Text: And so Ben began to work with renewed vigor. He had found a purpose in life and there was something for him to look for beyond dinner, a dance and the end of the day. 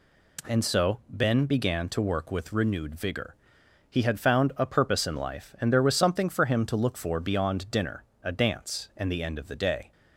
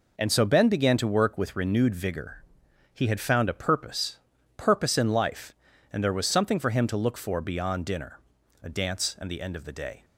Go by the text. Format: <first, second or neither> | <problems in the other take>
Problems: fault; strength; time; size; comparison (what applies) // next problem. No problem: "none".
first | says "purpose" twice; at 4.5 s